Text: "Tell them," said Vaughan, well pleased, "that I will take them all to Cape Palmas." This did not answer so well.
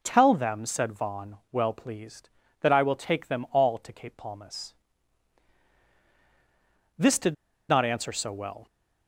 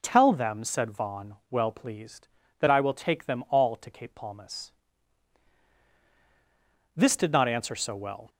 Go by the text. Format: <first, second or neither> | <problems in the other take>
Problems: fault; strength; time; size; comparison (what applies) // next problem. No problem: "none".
second | pauses between "did" and "not"; slight; at 7.3 s; 0.35 s long